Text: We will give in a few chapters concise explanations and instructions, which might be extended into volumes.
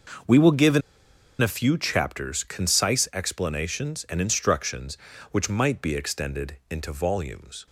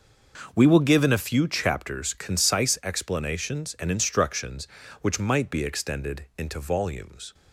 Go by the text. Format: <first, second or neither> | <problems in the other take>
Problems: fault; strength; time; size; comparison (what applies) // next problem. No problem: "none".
second | pauses between "in" and "a"; noticeable; at 0.8 s; 0.61 s long